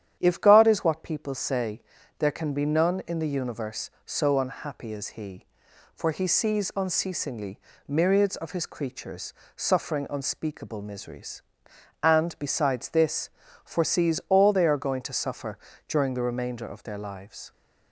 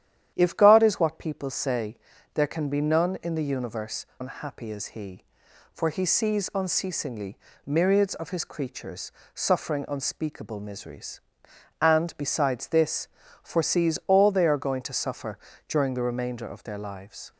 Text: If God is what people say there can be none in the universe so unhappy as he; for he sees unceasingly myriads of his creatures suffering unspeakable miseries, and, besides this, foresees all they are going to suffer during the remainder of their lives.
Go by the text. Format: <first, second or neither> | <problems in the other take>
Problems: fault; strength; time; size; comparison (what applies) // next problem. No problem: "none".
first | starts louder than the rest; strong; until 1.3 s; 10.5 dB; strong in the first // pauses between "say" and "there"; at 1.9 s; 0.38 s long; also in the first // skips "so"; at 4.1 s // pauses between "unceasingly" and "myriads"; slight; at 7.3 s; 0.28 s long; slight in the first // pauses between "creatures" and "suffering"; slight; at 9.1 s; 0.24 s long; slight in the first // pauses between "suffer" and "during"; slight; at 15.3 s; 0.30 s long; slight in the first